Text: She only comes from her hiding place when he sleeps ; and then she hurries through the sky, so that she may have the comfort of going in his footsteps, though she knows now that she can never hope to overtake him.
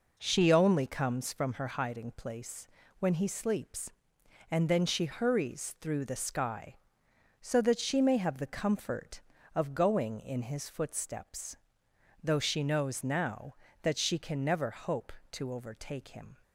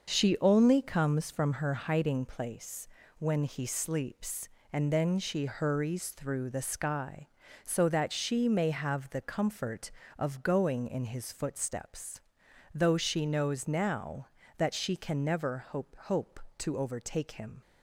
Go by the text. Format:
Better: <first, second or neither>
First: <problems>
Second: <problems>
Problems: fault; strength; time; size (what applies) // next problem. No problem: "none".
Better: first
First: pauses between "place" and "when"; slight; at 2.6 s; 0.32 s long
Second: starts louder than the rest; until 1.1 s; 6 dB // pauses between "place" and "when"; slight; at 2.8 s; 0.30 s long // says "hope" twice; at 15.9 s